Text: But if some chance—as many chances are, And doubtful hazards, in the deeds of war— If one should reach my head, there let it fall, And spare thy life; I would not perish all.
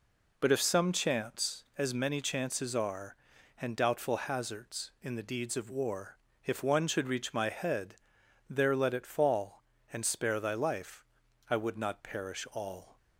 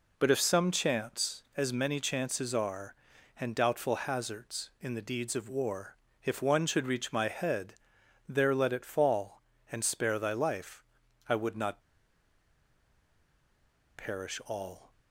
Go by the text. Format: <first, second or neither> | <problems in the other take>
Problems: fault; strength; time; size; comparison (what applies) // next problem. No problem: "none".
first | pauses between "not" and "perish"; strong; at 11.8 s; 2.1 s long